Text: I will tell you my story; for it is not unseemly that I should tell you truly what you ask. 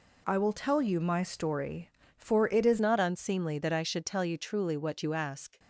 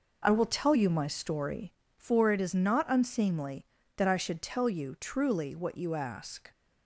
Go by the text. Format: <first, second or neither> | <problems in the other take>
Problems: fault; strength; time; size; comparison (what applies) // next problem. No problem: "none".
second | changes voice at "not"; from 2.7 s on; 2.8 s long